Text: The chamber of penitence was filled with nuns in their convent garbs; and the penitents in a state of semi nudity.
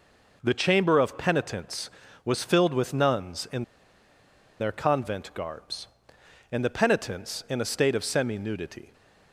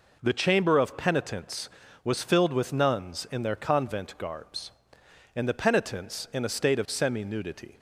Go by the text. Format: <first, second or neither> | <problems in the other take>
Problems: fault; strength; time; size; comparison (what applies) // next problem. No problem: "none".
second | pauses between "in" and "their"; noticeable; at 3.6 s; 0.96 s long